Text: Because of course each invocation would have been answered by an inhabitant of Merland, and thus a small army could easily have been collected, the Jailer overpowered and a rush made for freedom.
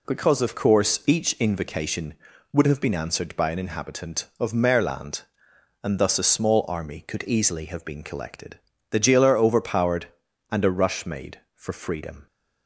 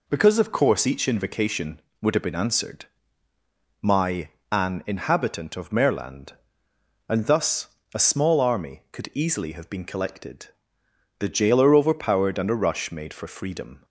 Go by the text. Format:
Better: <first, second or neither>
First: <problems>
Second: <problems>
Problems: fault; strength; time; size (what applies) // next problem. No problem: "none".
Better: first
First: none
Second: says "my" for "by"; at 3.8 s // pauses between "thus" and "a"; slight; at 7.6 s; 0.26 s long